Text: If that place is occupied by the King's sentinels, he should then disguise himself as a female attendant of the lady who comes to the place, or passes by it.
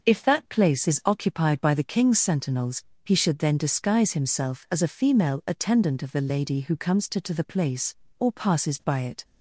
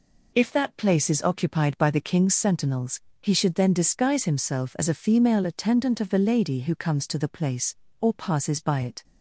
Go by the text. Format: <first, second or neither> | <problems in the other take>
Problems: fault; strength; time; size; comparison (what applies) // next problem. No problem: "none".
second | says "to" twice; at 7.2 s